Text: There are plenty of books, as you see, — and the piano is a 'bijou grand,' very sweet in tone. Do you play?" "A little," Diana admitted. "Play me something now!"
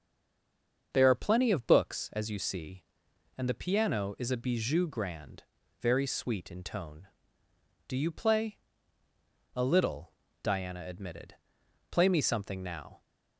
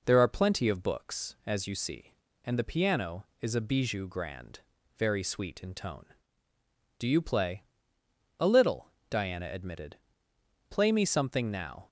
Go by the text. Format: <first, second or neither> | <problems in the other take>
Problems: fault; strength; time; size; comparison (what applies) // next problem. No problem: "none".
second | stays silent before the first word; slight; until 0.9 s; 0.9 s long // starts louder than the rest; until 1.9 s; 6.5 dB